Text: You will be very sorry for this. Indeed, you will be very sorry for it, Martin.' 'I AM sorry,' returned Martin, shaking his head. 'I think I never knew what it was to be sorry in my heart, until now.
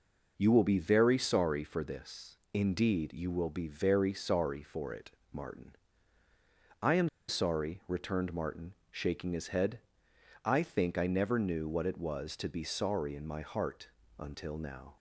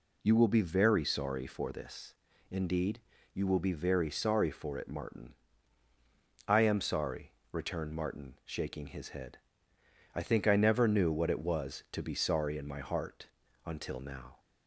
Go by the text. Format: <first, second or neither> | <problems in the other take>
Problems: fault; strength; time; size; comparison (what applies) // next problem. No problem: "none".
second | pauses between "AM" and "sorry"; slight; at 7.0 s; 0.21 s long